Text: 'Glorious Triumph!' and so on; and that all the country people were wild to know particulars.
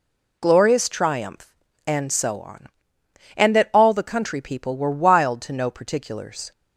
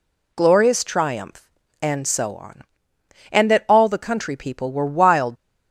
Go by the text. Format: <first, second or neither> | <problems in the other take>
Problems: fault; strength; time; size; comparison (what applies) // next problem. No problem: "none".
first | stops before "to know particulars"; at 5.3 s